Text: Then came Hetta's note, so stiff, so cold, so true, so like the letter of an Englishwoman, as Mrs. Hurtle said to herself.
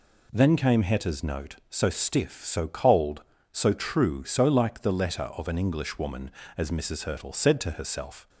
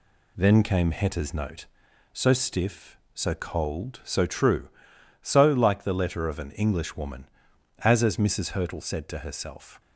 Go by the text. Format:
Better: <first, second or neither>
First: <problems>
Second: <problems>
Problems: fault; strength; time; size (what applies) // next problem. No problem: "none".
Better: first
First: none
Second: says "as" twice; at 8.0 s